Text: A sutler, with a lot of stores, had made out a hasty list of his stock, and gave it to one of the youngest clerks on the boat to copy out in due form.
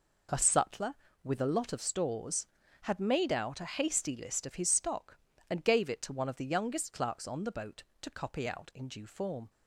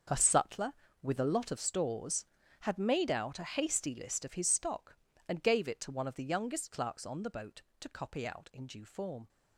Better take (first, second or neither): first